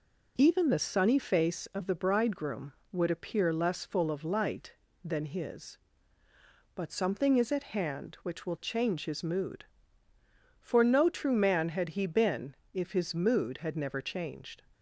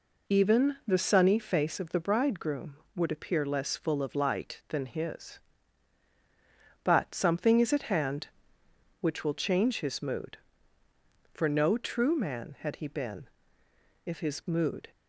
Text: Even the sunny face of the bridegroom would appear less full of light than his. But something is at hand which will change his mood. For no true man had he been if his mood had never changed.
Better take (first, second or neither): first